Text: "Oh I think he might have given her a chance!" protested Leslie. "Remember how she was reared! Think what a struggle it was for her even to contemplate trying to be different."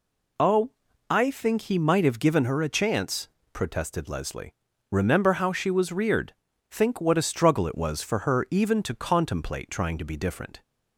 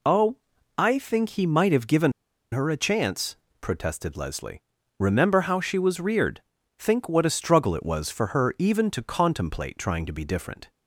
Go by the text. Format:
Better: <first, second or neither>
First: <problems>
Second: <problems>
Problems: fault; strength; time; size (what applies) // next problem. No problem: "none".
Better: first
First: pauses between "Oh" and "I"; at 0.6 s; 0.40 s long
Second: pauses between "Oh" and "I"; at 0.3 s; 0.42 s long // pauses between "given" and "her"; at 2.1 s; 0.41 s long